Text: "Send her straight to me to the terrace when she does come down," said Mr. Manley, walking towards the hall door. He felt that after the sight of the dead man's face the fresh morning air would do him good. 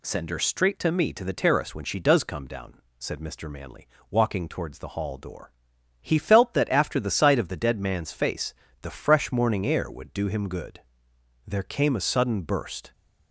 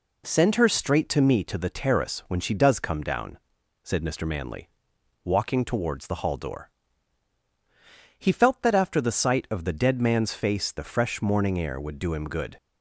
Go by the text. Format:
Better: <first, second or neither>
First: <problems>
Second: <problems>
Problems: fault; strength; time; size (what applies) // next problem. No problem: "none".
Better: second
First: pauses between "face" and "the"; slight; at 8.5 s; 0.26 s long // goes on to say "There came a sudden burst"; from 11.4 s on; 1.4 s long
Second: none